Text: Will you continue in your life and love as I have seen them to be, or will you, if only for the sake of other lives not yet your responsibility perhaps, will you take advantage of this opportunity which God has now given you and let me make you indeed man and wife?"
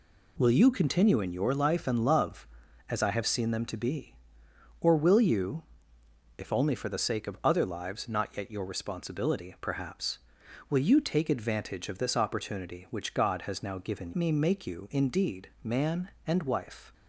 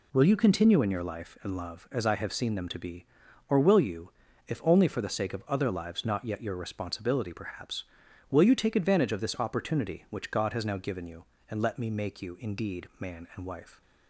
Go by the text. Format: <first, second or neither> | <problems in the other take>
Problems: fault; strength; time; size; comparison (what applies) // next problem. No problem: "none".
second | skips "you and let"; at 14.1 s